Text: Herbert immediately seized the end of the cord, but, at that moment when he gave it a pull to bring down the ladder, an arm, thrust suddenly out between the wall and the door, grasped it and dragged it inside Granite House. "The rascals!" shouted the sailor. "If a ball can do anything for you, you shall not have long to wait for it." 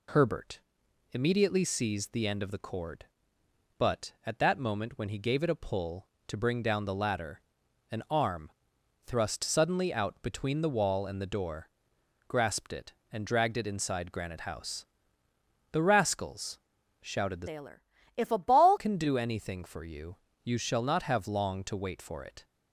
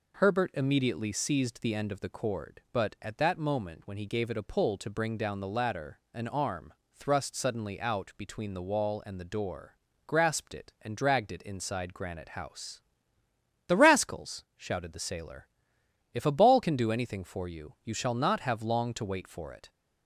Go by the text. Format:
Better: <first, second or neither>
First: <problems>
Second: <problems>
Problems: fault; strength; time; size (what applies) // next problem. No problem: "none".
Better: second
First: pauses between "Herbert" and "immediately"; noticeable; at 0.5 s; 0.52 s long // changes voice from "sailor" to "ball"; from 17.4 to 18.7 s; 1.3 s long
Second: none